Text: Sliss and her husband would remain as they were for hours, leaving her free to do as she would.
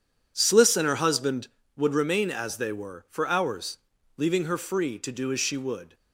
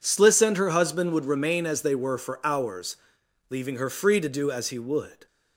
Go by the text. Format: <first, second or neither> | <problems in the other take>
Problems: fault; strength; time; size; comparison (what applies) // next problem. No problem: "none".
first | says "he" for "she"; at 4.7 s